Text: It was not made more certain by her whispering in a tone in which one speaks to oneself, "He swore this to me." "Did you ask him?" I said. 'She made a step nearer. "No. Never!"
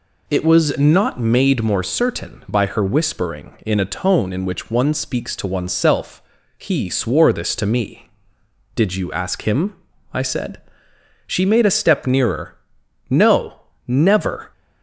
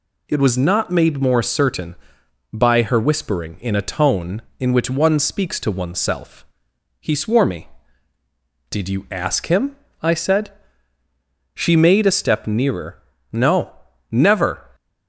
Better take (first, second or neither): first